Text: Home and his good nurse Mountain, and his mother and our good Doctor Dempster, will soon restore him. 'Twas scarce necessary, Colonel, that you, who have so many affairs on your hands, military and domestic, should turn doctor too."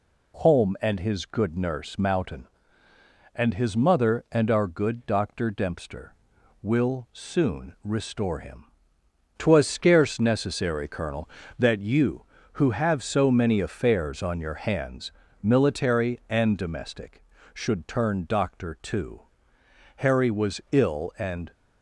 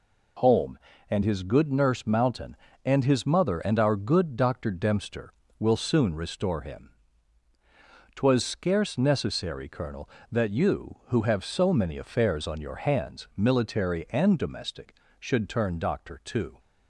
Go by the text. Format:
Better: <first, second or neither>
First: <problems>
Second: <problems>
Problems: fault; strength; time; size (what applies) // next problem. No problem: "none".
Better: second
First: goes on to say "Harry was ill and"; from 19.9 s on; 1.5 s long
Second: none